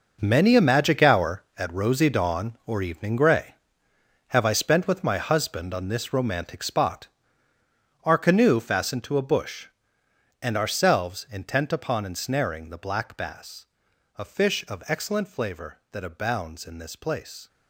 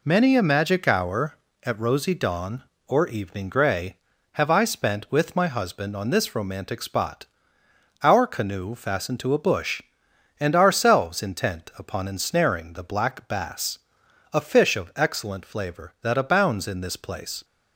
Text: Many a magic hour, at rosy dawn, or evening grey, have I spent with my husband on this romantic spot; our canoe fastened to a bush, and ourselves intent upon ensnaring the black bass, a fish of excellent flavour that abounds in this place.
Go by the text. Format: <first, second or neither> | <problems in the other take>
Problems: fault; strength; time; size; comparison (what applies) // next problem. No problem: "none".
second | gets quieter; strong; throughout; 12 dB